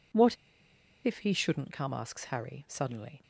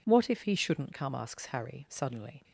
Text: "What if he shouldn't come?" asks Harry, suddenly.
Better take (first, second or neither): second